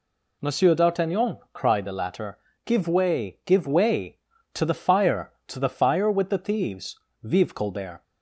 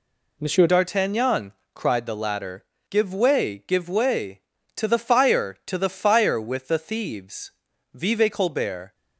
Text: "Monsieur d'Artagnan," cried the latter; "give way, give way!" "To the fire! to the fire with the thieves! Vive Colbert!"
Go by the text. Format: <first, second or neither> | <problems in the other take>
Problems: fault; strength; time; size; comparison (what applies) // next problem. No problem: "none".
first | changes voice at "d'Artagnan"; from 0.6 s on; 8.3 s long